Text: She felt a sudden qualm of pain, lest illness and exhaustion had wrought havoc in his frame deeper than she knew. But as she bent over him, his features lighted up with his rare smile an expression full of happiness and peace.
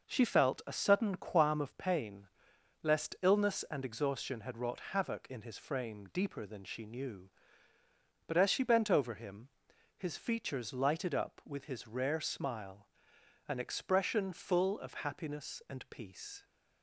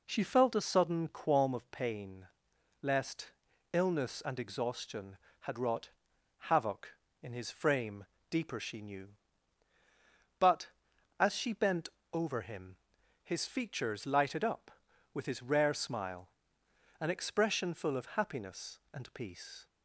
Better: first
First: pauses between "smile" and "an"; noticeable; at 12.8 s; 0.58 s long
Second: pauses between "lest" and "illness"; at 3.3 s; 0.40 s long // pauses between "wrought" and "havoc"; noticeable; at 5.8 s; 0.52 s long // pauses between "frame" and "deeper"; slight; at 8.0 s; 0.24 s long // skips "than"; at 8.5 s // pauses between "bent" and "over"; slight; at 11.8 s; 0.26 s long // pauses between "smile" and "an"; noticeable; at 16.2 s; 0.72 s long

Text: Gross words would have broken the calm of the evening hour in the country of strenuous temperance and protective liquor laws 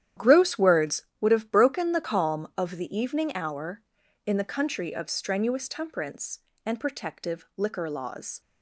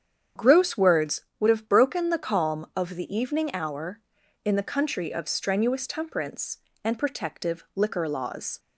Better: second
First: gets quieter; strong; throughout; 12 dB // starts louder than the rest; strong; until 1.3 s; 10.5 dB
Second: starts louder than the rest; strong; until 1.5 s; 8.5 dB

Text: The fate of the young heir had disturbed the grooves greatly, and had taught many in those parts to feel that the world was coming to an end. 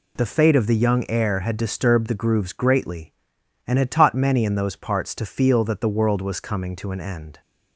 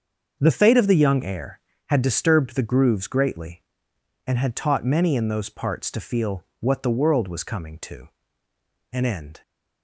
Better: first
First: none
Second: starts louder than the rest; until 1.4 s; 6.5 dB // says "what" for "that"; at 6.5 s // pauses between "to" and "an"; noticeable; at 8.0 s; 0.84 s long

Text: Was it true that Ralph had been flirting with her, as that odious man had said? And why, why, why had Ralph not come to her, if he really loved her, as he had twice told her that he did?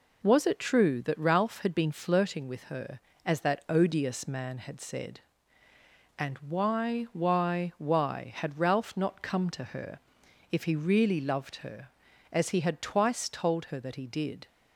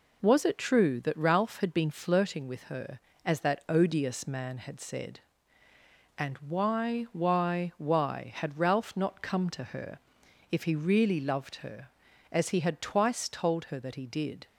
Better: neither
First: none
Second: none

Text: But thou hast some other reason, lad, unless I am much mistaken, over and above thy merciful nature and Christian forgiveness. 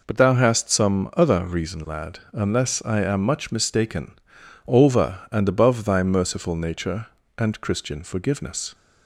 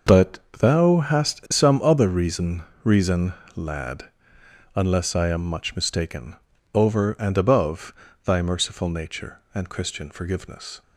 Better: first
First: none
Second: starts louder than the rest; until 1.2 s; 6 dB // pauses between "But" and "thou"; slight; at 0.3 s; 0.20 s long // says "reason" twice; at 2.8 s // pauses between "above" and "thy"; slight; at 7.9 s; 0.32 s long

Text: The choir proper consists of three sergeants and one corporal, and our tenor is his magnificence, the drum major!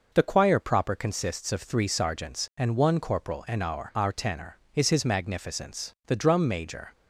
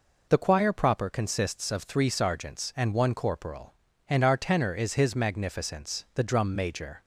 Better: second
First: says "our" twice; at 3.9 s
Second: none

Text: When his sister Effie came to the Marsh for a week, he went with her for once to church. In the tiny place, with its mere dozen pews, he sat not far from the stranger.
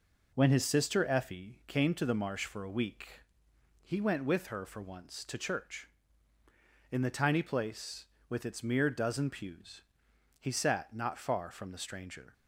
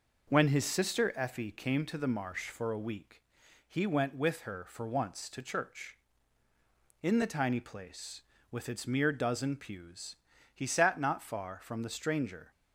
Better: neither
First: none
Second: none

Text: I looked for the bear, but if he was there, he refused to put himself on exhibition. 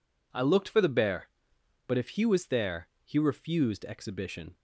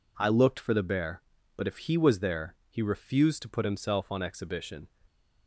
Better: second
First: skips "to put himself on"; at 3.8 s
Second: none

